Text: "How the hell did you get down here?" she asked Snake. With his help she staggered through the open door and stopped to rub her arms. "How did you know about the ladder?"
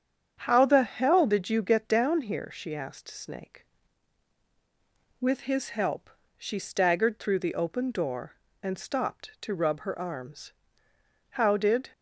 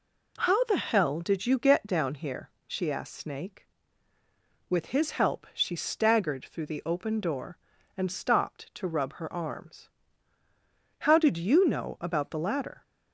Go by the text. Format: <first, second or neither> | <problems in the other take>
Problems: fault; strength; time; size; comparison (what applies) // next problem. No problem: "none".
second | starts louder than the rest; strong; until 1.4 s; 8 dB // pauses between "help" and "she"; slight; at 6.0 s; 0.28 s long // stops before "you know about the ladder"; at 11.9 s